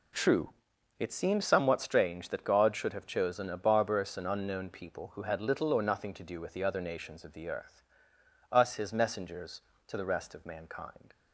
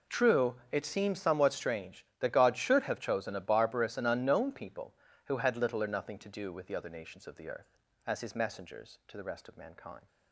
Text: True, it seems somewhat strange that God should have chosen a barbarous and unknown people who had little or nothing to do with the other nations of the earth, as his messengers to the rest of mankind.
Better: second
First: says "us" for "as"; at 8.5 s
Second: none

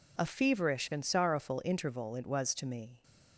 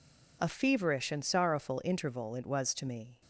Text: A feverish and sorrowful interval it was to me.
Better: neither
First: none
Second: none

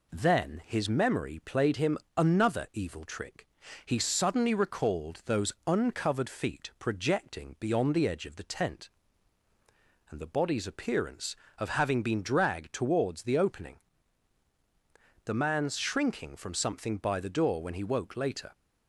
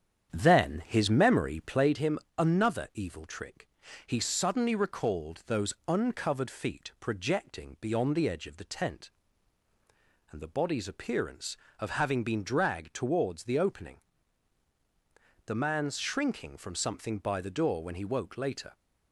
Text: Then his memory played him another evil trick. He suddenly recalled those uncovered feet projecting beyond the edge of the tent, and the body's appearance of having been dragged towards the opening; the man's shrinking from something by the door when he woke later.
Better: first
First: pauses between "him" and "another"; slight; at 1.9 s; 0.20 s long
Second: starts louder than the rest; strong; until 2.0 s; 8.5 dB // pauses between "him" and "another"; slight; at 2.1 s; 0.20 s long

